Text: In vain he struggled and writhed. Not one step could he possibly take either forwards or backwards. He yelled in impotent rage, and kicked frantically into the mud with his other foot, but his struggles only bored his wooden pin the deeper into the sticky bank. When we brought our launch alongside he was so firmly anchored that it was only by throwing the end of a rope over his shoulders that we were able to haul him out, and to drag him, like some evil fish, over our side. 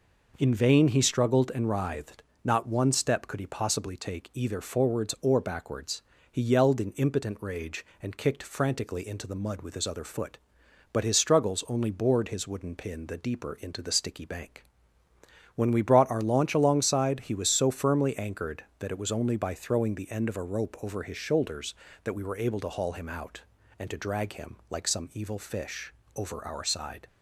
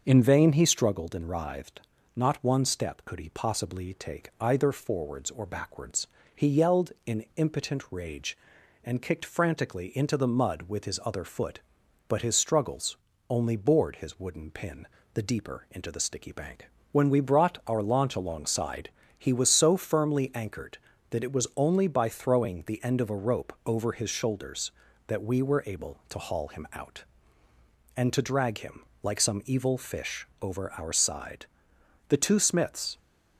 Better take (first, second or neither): first